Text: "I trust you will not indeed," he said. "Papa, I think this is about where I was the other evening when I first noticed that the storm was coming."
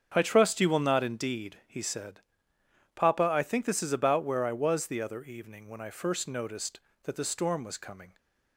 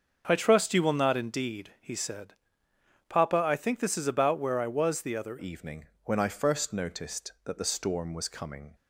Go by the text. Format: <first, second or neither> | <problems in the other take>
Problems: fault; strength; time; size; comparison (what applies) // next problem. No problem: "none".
first | starts louder than the rest; until 1.2 s; 6.5 dB; strong in the first // changes voice at "evening"; from 5.3 s on; 3.4 s long // pauses between "evening" and "when"; slight; at 5.8 s; 0.20 s long